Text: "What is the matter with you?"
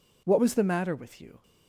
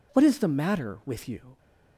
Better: second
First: says "was" for "is"; at 0.4 s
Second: none

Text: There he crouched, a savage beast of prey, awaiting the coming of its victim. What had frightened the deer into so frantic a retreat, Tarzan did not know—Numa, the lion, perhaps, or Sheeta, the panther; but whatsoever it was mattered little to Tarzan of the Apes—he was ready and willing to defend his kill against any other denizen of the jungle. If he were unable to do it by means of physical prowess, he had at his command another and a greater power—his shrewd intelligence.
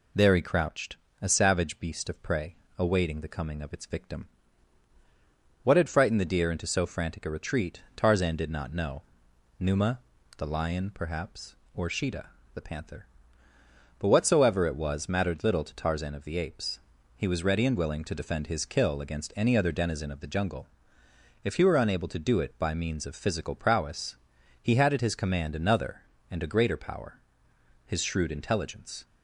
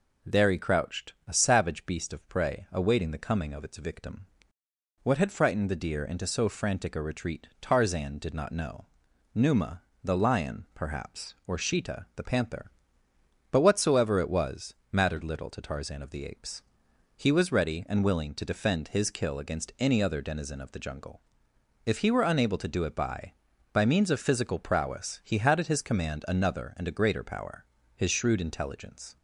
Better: first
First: none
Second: pauses between "was" and "mattered"; slight; at 14.7 s; 0.18 s long // says "by" twice; at 23.7 s

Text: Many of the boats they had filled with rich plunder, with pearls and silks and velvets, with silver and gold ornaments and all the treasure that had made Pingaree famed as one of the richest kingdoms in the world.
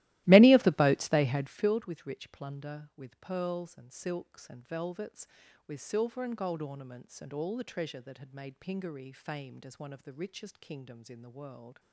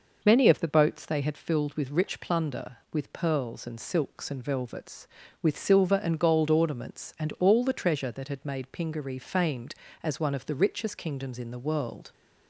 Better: second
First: starts louder than the rest; strong; until 1.7 s; 16.5 dB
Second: none

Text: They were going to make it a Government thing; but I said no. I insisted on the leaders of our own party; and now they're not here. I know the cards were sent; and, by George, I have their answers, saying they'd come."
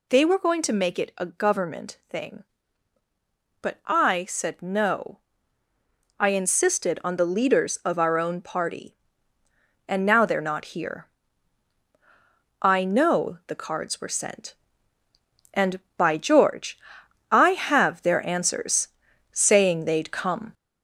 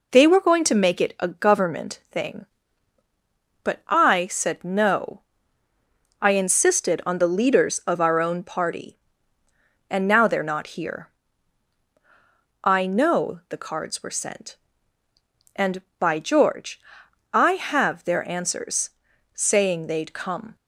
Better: second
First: gets louder; throughout; 4 dB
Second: none

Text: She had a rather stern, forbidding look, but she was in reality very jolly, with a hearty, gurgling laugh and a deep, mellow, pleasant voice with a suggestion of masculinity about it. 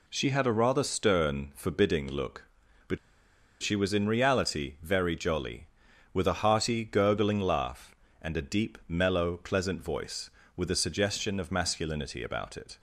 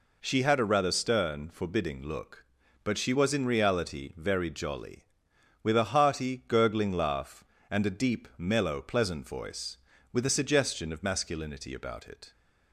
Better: second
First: pauses between "but" and "she"; noticeable; at 2.9 s; 0.65 s long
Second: none

